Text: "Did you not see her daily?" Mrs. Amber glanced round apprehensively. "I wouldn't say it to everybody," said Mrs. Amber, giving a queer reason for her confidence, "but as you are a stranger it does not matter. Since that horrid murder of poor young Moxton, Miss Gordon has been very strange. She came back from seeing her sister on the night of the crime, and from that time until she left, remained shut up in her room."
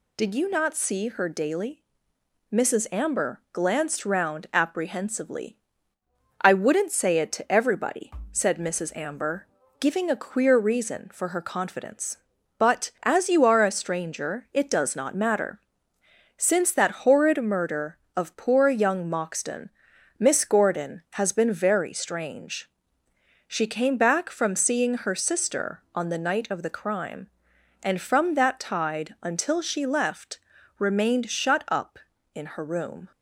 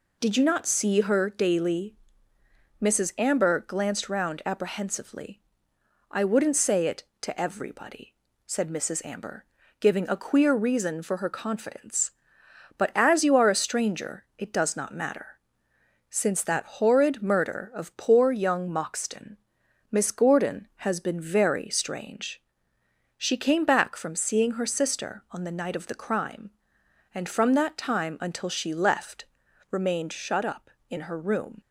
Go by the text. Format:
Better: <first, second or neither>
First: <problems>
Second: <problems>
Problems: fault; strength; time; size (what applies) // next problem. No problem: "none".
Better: second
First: says "tide" for "time"; at 28.5 s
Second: none